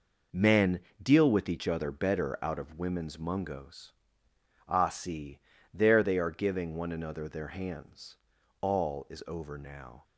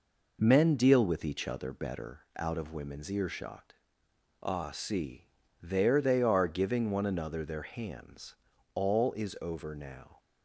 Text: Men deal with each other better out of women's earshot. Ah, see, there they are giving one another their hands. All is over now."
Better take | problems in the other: second | pauses between "Men" and "deal"; slight; at 0.8 s; 0.22 s long // says "mungos" for "earshot"; at 3.1 s

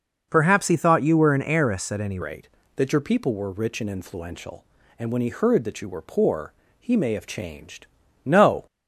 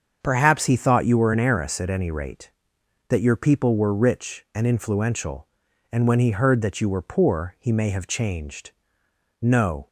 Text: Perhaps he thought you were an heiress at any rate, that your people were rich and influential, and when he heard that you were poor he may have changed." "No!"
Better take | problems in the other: second | starts louder than the rest; noticeable; until 1.3 s; 6 dB; also in the second // changes voice at "rate"; from 2.2 s on; 6.4 s long // pauses between "poor" and "he"; slight; at 6.5 s; 0.28 s long

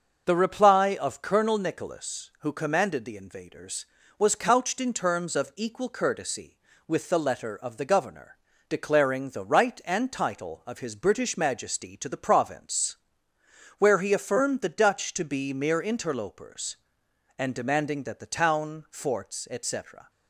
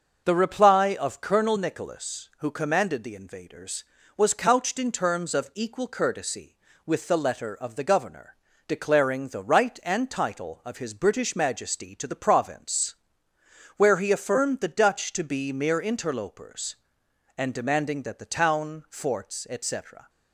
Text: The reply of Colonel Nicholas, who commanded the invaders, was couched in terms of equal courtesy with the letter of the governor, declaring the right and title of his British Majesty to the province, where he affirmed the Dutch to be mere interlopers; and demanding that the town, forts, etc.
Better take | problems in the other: neither | starts louder than the rest; the same in both

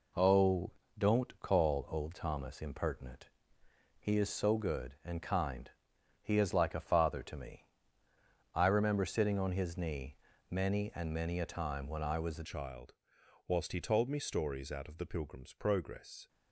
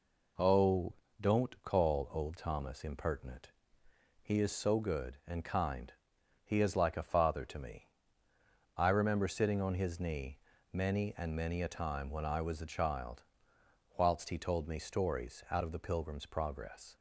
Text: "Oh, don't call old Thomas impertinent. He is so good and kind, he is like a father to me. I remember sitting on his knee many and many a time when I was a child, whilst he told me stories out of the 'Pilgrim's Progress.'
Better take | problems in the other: second | pauses between "knee" and "many"; slight; at 10.1 s; 0.34 s long; slight in the second // changes voice at "child"; from 12.4 s on; 3.8 s long

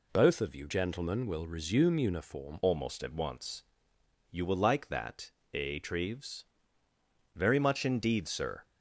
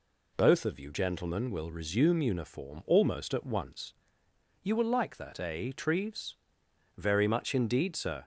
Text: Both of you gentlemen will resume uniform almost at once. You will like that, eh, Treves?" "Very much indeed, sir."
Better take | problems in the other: second | changes voice at "almost"; from 2.6 s on; 6.0 s long

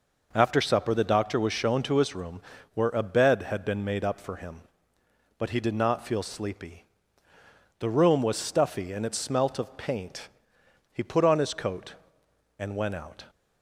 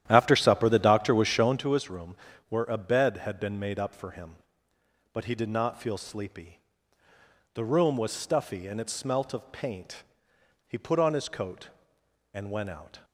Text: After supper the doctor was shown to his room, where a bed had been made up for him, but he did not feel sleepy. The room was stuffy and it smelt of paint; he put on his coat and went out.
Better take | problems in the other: first | starts louder than the rest; strong; until 1.6 s; 11.5 dB

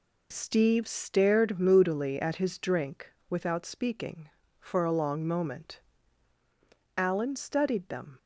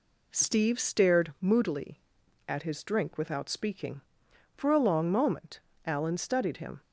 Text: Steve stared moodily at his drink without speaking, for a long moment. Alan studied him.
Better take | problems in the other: second | pauses between "drink" and "without"; slight; at 3.1 s; 0.16 s long // says "them" for "him"; at 7.8 s

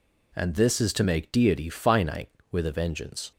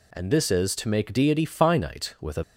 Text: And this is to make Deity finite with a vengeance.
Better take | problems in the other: first | stops before "vengeance"; at 2.4 s

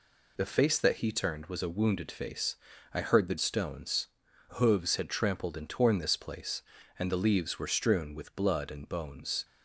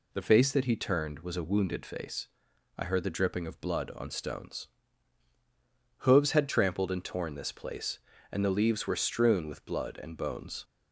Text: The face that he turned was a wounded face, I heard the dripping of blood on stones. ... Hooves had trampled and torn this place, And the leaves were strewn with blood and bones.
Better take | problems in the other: second | skips "dripping of blood on"; at 3.3 s

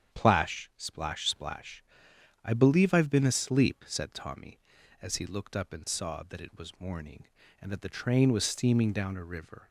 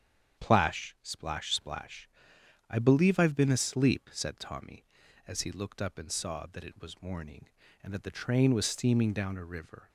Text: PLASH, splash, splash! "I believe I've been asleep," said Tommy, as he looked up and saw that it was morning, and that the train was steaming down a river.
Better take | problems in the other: neither | starts louder than the rest; strong; the same in both

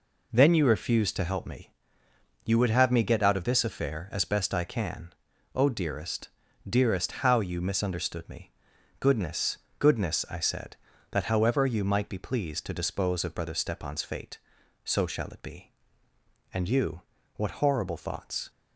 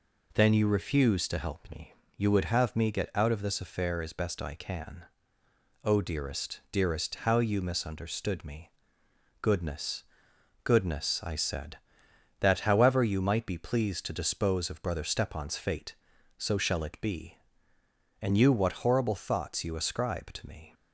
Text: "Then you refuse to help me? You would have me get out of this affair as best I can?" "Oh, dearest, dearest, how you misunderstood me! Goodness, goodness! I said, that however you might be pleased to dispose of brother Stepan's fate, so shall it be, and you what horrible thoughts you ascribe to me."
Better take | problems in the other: second | pauses between "you" and "what"; slight; at 17.0 s; 0.34 s long // stops before "you ascribe to me"; at 18.4 s

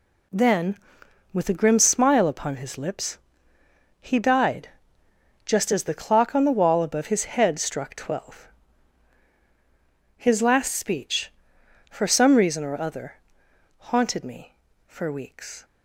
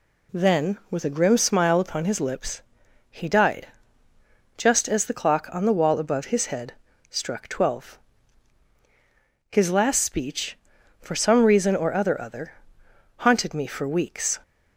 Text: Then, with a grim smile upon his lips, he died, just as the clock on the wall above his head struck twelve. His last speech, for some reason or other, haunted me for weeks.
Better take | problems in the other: first | pauses between "head" and "struck"; at 6.7 s; 0.38 s long // says "other" twice; at 12.2 s

